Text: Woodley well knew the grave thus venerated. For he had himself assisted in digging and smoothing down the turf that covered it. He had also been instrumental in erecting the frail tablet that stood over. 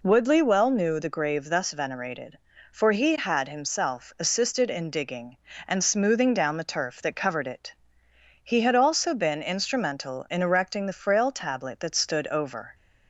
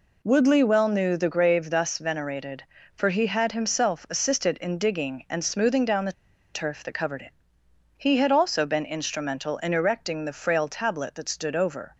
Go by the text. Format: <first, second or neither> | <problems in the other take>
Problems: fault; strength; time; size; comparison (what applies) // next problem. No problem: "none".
first | pauses between "the" and "turf"; at 6.1 s; 0.41 s long